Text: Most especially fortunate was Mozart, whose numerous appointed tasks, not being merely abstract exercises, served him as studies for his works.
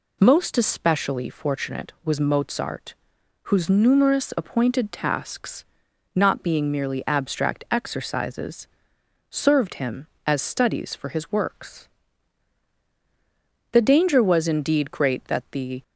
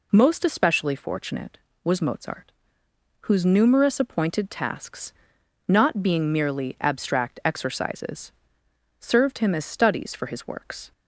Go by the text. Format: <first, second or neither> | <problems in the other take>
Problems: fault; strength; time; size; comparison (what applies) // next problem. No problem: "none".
second | goes on to say "The danger was indeed great that the"; strong; from 13.7 s on; 2.1 s long